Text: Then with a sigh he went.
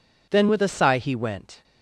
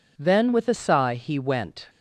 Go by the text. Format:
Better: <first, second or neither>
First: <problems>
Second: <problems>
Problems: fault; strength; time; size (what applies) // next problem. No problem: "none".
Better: neither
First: none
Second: none